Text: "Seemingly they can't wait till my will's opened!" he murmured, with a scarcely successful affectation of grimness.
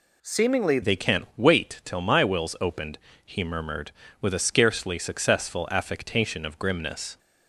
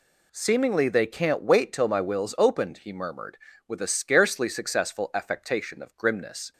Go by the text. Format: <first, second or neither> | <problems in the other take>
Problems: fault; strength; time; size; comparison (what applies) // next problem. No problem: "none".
second | changes voice at "they"; from 0.8 s on; 6.3 s long